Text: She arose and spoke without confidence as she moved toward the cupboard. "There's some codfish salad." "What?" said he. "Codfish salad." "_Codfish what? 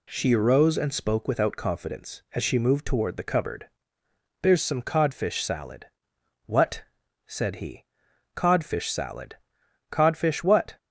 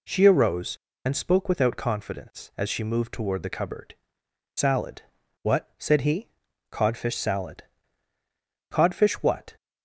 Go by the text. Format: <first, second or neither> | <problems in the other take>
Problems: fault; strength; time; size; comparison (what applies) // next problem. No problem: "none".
first | skips "There's some codfish"; at 4.2 s